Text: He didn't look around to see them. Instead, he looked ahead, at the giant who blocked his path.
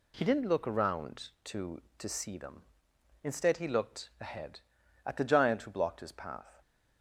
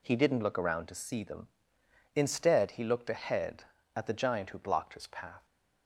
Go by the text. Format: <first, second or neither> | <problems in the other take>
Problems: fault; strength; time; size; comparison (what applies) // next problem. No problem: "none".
second | says "to" twice; at 1.9 s